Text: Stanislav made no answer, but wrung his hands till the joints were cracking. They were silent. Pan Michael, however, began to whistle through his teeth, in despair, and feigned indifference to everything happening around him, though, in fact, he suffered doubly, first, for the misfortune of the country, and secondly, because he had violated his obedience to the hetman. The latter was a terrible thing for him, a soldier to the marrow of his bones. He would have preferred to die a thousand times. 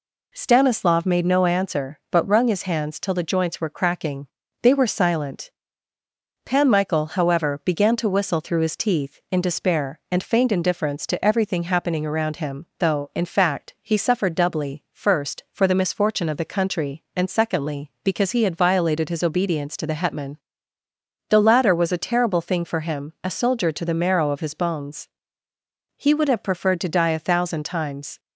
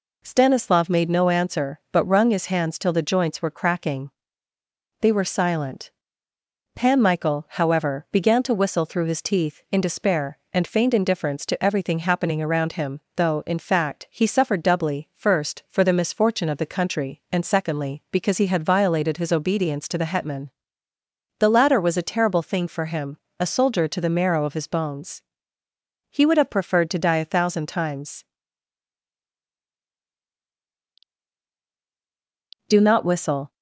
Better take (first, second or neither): first